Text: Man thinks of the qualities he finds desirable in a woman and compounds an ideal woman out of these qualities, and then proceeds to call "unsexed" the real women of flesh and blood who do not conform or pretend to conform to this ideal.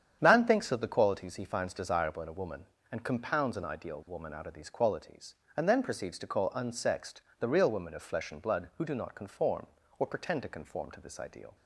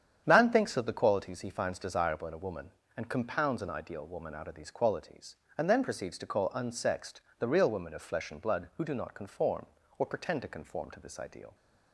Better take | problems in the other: neither | starts louder than the rest; strong; the same in both // pauses between "unsexed" and "the"; slight; the same in both

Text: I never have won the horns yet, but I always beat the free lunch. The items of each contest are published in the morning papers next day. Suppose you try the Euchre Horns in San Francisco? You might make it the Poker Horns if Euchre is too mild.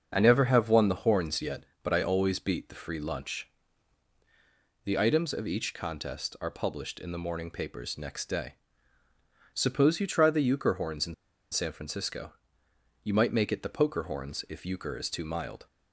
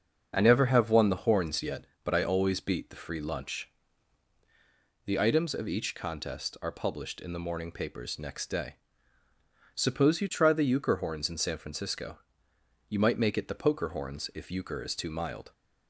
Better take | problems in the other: second | starts louder than the rest; until 1.1 s; 6.5 dB; also in the second // pauses between "in" and "San"; at 11.1 s; 0.37 s long

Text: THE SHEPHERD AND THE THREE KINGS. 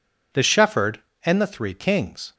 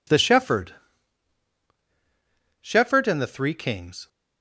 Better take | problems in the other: first | says "SHEPHERD" twice; at 2.6 s

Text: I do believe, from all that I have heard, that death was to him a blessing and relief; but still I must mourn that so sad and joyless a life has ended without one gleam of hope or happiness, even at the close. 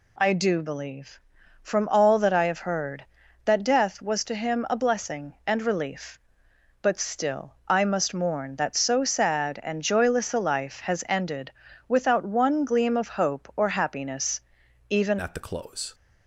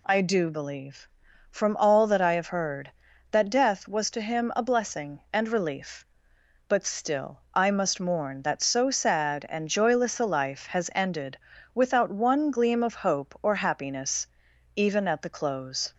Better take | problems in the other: second | pauses between "ended" and "without"; slight; at 11.5 s; 0.36 s long; slight in the second // changes voice at "at"; from 15.2 s on; 0.7 s long

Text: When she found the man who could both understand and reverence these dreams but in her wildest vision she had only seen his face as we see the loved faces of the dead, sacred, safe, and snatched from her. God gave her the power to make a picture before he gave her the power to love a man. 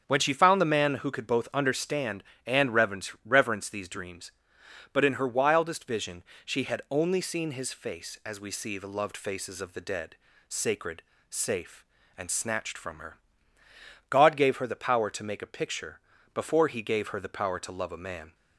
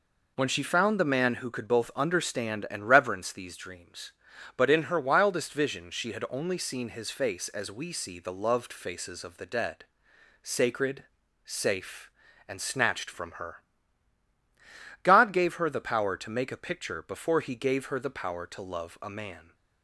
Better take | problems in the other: second | starts louder than the rest; strong; until 1.0 s; 7.5 dB // says "reverence" twice; at 3.2 s // pauses between "vision" and "she"; slight; at 6.2 s; 0.22 s long // pauses between "picture" and "before"; slight; at 16.0 s; 0.32 s long

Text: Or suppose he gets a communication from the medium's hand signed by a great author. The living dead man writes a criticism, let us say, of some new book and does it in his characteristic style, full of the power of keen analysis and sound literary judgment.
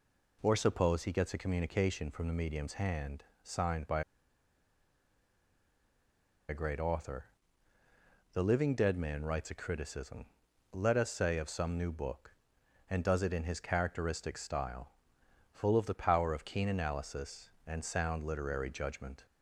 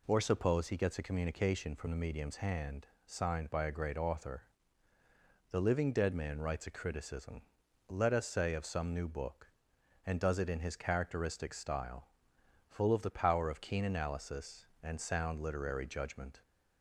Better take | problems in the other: second | pauses between "hand" and "signed"; slight; at 3.2 s; 0.18 s long; slight in the second // pauses between "by" and "a"; strong; at 4.0 s; 2.4 s long

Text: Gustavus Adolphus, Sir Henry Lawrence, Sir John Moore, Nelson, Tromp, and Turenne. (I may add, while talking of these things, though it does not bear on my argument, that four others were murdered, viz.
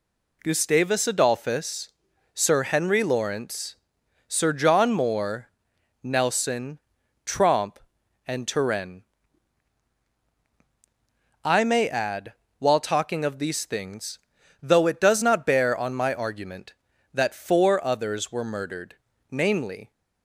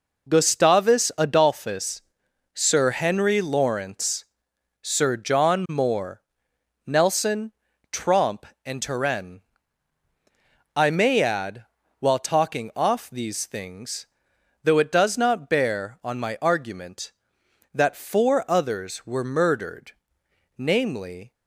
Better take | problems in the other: first | says "off" for "of"; at 12.7 s

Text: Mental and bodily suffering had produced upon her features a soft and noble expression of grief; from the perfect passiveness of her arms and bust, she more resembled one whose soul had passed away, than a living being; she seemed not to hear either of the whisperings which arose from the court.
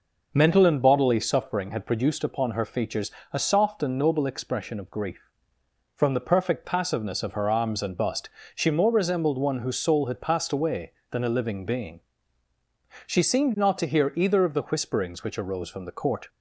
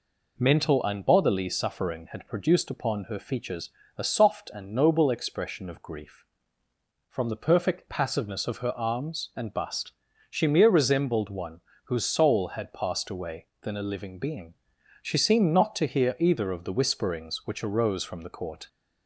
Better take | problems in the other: first | pauses between "features" and "a"; slight; at 3.7 s; 0.26 s long; slight in the first // says "mere" for "more"; at 10.4 s // pauses between "one" and "whose"; slight; at 11.6 s; 0.24 s long

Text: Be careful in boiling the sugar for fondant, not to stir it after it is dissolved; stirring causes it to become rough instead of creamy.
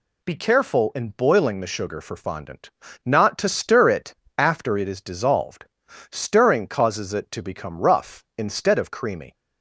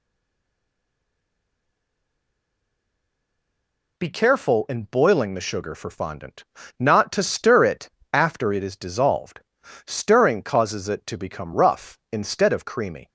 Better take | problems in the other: first | stays silent before the first word; strong; until 3.9 s; 3.9 s long // pauses between "it" and "after"; slight; at 7.8 s; 0.24 s long; slight in the first

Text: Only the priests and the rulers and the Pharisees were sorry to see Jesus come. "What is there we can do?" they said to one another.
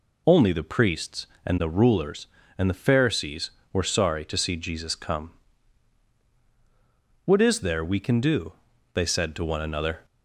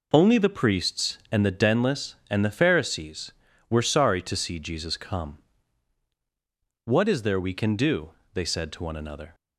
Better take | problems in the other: first | says "denless" for "rulers"; at 1.5 s

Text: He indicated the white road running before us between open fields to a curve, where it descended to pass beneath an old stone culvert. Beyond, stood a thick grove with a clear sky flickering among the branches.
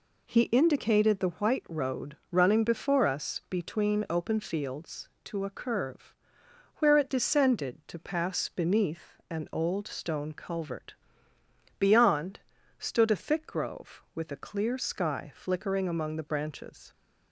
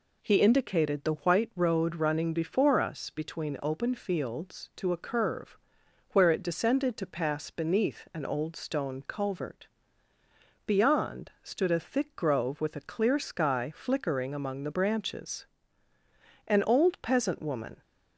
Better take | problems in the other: first | goes on to say "An old peasant woman"; from 16.4 s on; 1.3 s long

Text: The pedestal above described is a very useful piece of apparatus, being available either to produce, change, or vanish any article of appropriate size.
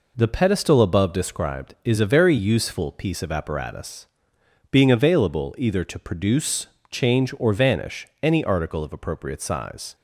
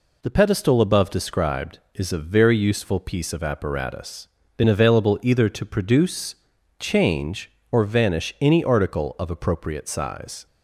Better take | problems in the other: first | says "been" for "being"; at 4.5 s

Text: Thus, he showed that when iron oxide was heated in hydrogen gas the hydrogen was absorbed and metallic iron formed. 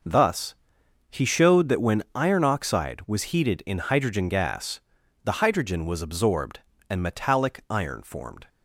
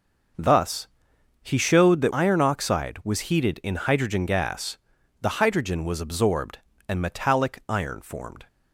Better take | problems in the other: first | skips "when"; at 2.1 s // pauses between "gas" and "the"; at 4.7 s; 0.44 s long; also in the first

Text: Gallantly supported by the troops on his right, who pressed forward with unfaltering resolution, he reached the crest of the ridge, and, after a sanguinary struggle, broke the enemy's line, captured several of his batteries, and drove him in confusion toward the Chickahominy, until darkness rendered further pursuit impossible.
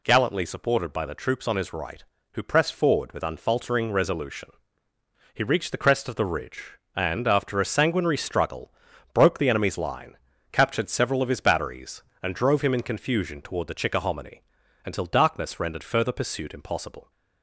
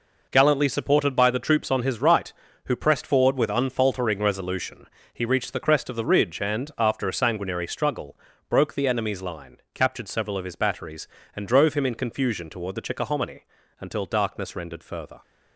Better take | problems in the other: first | stops before "pursuit impossible"; at 15.2 s

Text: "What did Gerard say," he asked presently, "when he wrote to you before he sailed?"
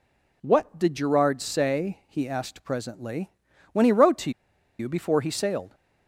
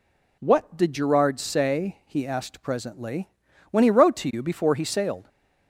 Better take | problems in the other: second | pauses between "to" and "you"; noticeable; at 4.2 s; 0.49 s long

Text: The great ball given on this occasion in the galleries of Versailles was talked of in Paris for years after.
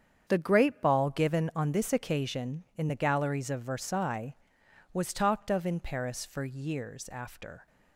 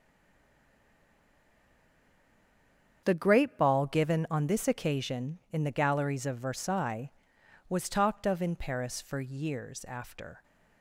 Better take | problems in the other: first | stays silent before the first word; strong; until 3.0 s; 3.0 s long // starts louder than the rest; strong; until 4.0 s; 7.5 dB; strong in the first

